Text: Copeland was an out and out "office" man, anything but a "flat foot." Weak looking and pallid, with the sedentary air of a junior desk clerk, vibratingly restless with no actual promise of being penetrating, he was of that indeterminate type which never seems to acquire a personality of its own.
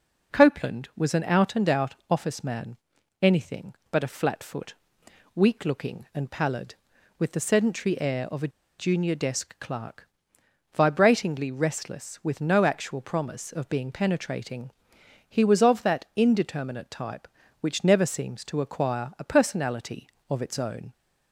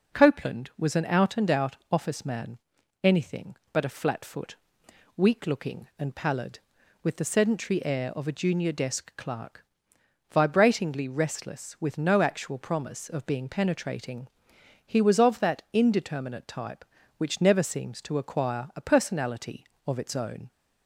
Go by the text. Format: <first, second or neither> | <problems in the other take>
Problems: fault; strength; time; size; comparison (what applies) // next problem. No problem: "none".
second | pauses between "a" and "junior"; slight; at 8.4 s; 0.29 s long